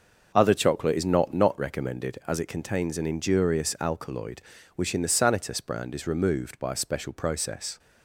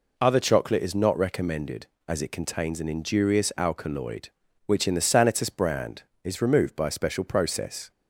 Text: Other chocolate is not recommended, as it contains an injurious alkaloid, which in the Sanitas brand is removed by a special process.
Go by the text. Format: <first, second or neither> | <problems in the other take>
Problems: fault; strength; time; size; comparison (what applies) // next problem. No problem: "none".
second | starts louder than the rest; noticeable; until 1.3 s; 6 dB // says "not" twice; at 1.3 s